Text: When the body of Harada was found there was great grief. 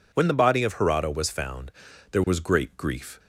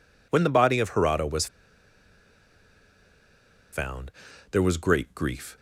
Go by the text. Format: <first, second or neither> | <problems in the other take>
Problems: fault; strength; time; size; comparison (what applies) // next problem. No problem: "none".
first | pauses between "was" and "found"; strong; at 1.4 s; 2.2 s long // pauses between "found" and "there"; at 4.0 s; 0.40 s long; also in the first